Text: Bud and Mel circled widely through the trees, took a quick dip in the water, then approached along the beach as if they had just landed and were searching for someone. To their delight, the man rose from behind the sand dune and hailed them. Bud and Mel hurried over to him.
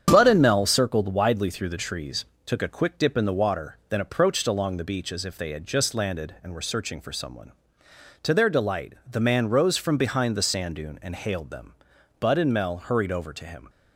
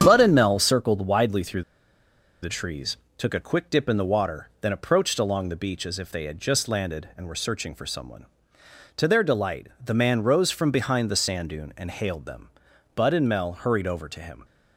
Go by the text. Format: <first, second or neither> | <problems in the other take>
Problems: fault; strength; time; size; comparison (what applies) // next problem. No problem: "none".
first | starts louder than the rest; strong; until 1.0 s; 8 dB; strong in the first // pauses between "through" and "the"; noticeable; at 1.6 s; 0.80 s long